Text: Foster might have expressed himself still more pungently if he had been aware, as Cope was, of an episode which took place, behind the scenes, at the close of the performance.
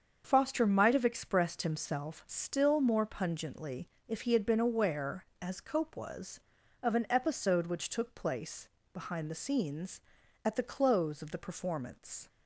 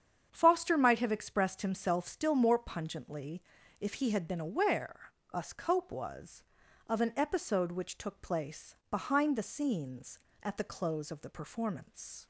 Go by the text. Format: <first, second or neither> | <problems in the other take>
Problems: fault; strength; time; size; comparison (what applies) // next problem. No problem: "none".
first | starts louder than the rest; strong; until 1.3 s; 8 dB; also in the first // pauses between "pungently" and "if"; at 3.4 s; 0.38 s long; slight in the first // says "us" for "as"; at 5.3 s